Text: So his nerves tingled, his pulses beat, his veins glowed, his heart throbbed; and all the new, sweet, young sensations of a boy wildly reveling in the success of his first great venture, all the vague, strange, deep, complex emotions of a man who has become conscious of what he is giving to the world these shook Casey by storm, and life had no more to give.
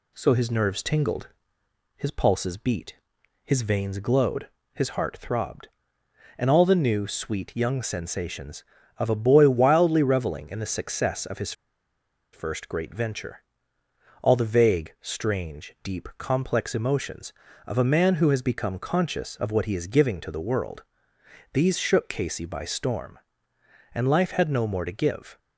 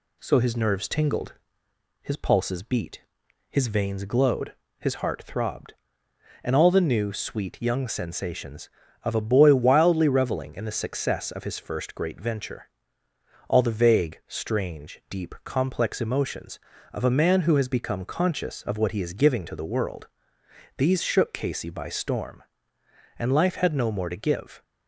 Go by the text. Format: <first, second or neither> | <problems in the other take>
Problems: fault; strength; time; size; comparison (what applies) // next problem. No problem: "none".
second | pauses between "his" and "first"; noticeable; at 11.5 s; 0.81 s long // pauses between "world" and "these"; noticeable; at 20.8 s; 0.70 s long; noticeable in the second